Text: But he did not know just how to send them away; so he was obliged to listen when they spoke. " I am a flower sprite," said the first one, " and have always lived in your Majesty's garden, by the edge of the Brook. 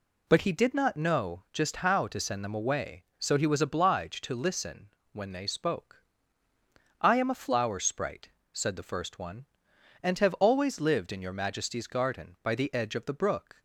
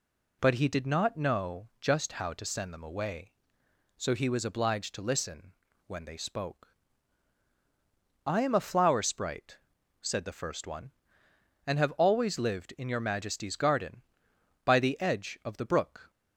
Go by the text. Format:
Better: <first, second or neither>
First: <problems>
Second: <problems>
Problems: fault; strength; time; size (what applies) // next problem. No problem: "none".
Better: neither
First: pauses between "listen" and "when"; slight; at 4.9 s; 0.24 s long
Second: pauses between "listen" and "when"; slight; at 5.5 s; 0.34 s long